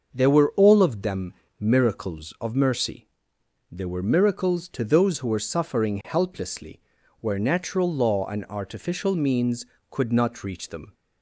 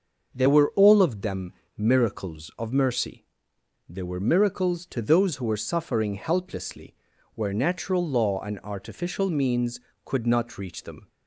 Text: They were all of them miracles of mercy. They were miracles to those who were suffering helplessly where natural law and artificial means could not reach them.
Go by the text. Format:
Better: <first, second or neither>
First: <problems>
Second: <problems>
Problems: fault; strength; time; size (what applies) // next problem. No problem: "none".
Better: neither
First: starts louder than the rest; until 1.1 s; 6.5 dB // pauses between "them" and "miracles"; slight; at 1.3 s; 0.28 s long // pauses between "helplessly" and "where"; at 6.7 s; 0.40 s long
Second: starts louder than the rest; until 1.3 s; 6.5 dB // pauses between "them" and "miracles"; slight; at 1.5 s; 0.26 s long // pauses between "helplessly" and "where"; at 6.9 s; 0.40 s long